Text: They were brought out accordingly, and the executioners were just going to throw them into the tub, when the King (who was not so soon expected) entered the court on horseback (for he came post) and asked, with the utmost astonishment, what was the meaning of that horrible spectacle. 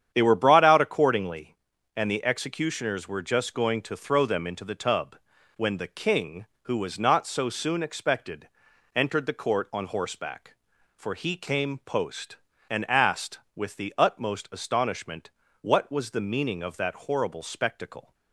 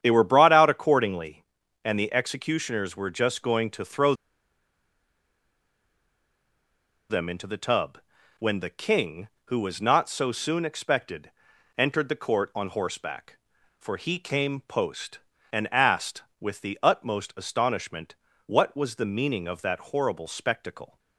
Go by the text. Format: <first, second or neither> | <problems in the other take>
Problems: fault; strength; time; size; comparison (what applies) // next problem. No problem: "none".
first | starts louder than the rest; strong; until 1.0 s; 9 dB; strong in the first // pauses between "throw" and "them"; strong; at 4.1 s; 2.9 s long